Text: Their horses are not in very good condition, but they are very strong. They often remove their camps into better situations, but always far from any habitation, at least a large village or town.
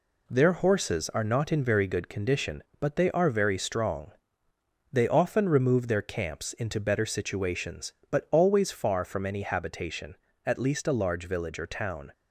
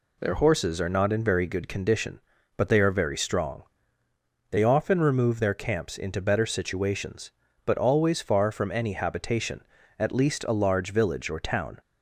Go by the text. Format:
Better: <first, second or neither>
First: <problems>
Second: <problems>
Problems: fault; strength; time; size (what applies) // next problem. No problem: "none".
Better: second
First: gets quieter; noticeable; throughout; 4.5 dB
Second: none